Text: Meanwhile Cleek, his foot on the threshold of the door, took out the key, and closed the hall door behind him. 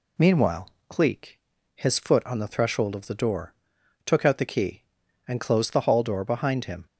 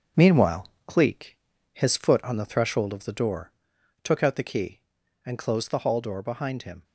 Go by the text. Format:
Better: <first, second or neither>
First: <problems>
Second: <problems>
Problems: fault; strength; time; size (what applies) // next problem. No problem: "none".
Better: first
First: pauses between "Meanwhile" and "Cleek"; slight; at 0.7 s; 0.16 s long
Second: gets quieter; noticeable; throughout; 5 dB // pauses between "Meanwhile" and "Cleek"; slight; at 0.6 s; 0.16 s long